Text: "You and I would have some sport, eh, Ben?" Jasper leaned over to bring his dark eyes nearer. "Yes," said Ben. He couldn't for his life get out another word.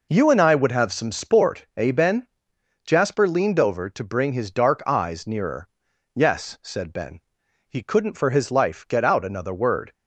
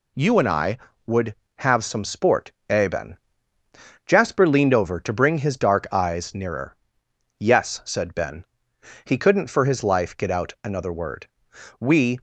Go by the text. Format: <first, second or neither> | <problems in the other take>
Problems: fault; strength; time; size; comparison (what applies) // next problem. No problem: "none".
first | goes on to say "We"; slight; from 11.8 s on; 0.40 s long